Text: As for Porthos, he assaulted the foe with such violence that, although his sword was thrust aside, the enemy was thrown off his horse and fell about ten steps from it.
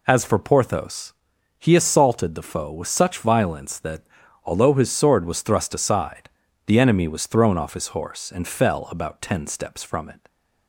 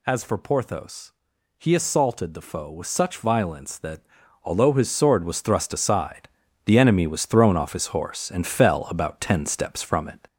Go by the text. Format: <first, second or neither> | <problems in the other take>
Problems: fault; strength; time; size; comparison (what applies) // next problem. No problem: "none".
first | gets louder; slight; throughout; 3 dB